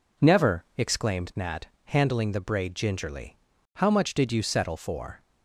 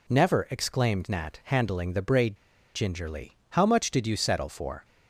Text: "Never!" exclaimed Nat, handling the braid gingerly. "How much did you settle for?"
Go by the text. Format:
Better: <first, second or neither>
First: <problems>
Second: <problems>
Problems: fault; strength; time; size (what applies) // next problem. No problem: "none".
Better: first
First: none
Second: pauses between "braid" and "gingerly"; at 2.3 s; 0.37 s long